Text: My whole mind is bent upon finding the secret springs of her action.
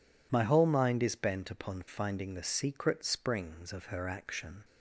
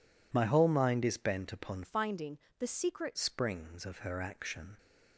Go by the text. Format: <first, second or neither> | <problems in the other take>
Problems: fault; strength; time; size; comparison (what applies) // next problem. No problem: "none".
first | changes voice from "finding" to "secret"; from 1.8 to 3.1 s; 1.3 s long // pauses between "finding" and "the"; slight; at 2.3 s; 0.22 s long